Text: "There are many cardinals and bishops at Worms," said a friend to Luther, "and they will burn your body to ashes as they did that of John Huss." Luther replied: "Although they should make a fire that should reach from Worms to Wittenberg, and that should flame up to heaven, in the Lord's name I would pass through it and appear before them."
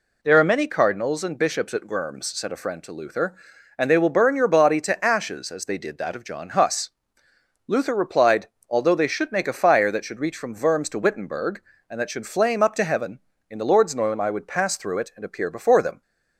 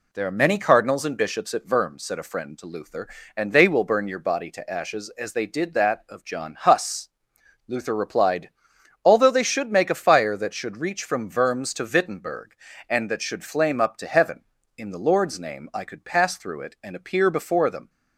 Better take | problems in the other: first | says "could" for "would"; at 15.8 s

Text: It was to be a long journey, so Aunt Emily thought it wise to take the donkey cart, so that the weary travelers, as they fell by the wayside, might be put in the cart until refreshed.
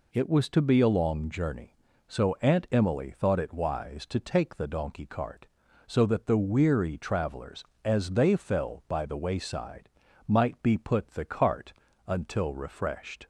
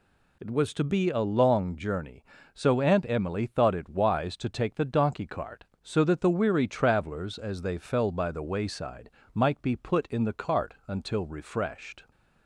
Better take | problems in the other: second | skips "in"; at 11.0 s // pauses between "cart" and "until"; slight; at 11.7 s; 0.34 s long

